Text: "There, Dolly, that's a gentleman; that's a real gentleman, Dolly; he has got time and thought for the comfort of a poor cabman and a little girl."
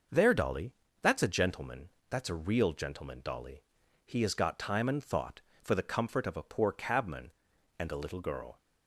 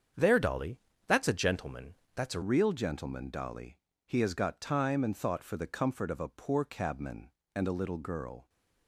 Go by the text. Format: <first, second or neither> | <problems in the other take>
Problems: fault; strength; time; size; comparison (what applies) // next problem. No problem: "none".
first | starts louder than the rest; strong; until 1.4 s; 7.5 dB; noticeable in the first // changes voice at "real"; from 2.4 s on; 6.0 s long